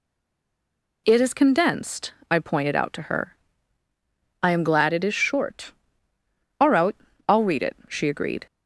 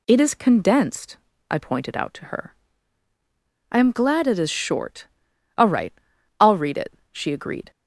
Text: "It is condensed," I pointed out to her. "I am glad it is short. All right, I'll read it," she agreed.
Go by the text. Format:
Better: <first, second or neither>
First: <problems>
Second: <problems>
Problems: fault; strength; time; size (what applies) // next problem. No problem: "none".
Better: second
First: stays silent before the first word; until 1.0 s; 1.0 s long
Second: none